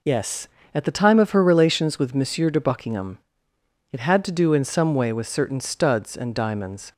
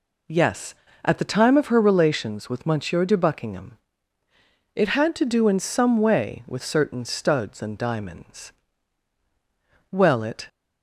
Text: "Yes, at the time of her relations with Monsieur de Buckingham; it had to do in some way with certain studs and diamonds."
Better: first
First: none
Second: goes on to say "Well it"; from 9.9 s on; 0.56 s long

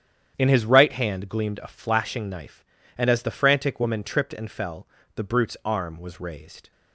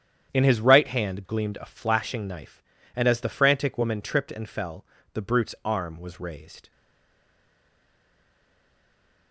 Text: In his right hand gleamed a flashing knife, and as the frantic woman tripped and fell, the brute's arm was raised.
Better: first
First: starts louder than the rest; strong; until 1.3 s; 9 dB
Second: starts louder than the rest; strong; until 1.3 s; 9 dB // stays silent after the last word; strong; from 6.7 s on; 2.6 s long

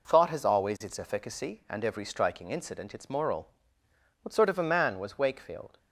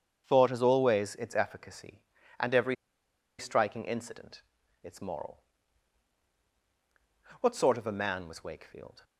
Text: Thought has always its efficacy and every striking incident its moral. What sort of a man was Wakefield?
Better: first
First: none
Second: starts louder than the rest; strong; until 1.2 s; 7.5 dB // pauses between "every" and "striking"; noticeable; at 2.7 s; 0.64 s long // pauses between "incident" and "its"; at 4.4 s; 0.42 s long

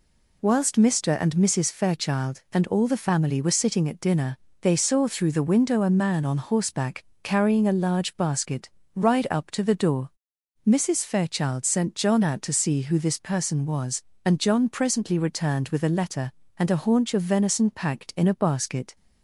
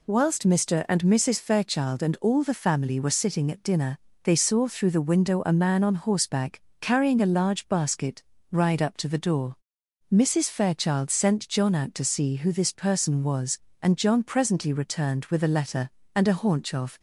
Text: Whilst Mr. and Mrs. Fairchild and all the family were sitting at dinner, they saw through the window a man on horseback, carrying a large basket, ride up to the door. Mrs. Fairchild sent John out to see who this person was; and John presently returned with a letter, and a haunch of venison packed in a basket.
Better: first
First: none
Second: stops before "venison packed in a basket"; at 16.9 s

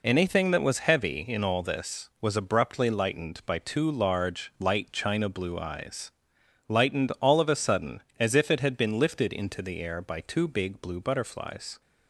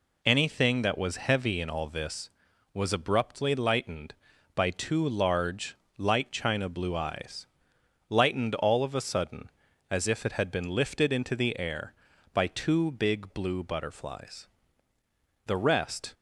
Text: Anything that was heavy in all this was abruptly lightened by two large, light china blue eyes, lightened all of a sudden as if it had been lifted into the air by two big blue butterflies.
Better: first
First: none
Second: goes on to say "The rest"; noticeable; from 15.4 s on; 0.66 s long

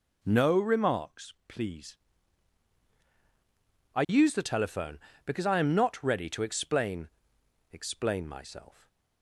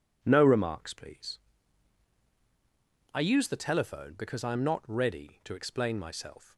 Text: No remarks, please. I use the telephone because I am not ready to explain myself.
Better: second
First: says "explain" twice; at 7.7 s // stays silent after the last word; slight; from 8.7 s on; 0.5 s long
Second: none

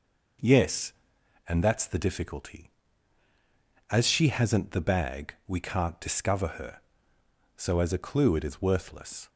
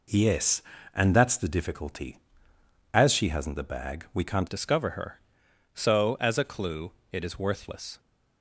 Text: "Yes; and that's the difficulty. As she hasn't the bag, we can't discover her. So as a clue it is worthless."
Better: first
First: none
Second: changes voice at "discover"; from 4.4 s on; 3.5 s long // pauses between "clue" and "it"; slight; at 6.9 s; 0.20 s long

